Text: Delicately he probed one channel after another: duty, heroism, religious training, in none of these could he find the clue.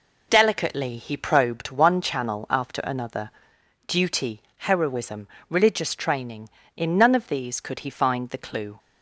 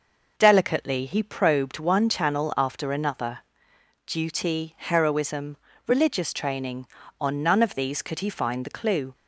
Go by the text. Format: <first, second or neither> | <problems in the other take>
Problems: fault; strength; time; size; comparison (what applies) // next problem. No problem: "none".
first | says "on" for "in"; at 7.2 s